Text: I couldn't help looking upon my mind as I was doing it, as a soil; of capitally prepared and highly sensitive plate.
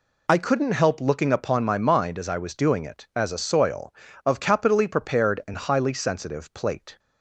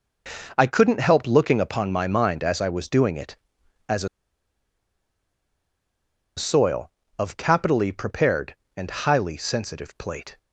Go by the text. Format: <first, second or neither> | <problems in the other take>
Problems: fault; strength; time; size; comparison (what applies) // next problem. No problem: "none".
first | pauses between "a" and "soil"; strong; at 4.0 s; 2.2 s long